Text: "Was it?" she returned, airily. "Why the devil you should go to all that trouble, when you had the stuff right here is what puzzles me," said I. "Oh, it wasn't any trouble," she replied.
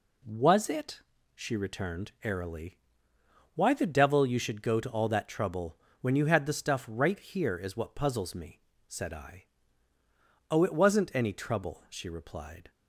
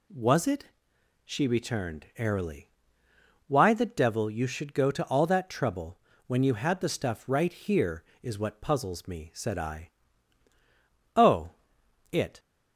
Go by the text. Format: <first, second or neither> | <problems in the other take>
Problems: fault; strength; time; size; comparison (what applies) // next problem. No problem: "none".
first | stops before "wasn't any trouble she replied"; at 12.3 s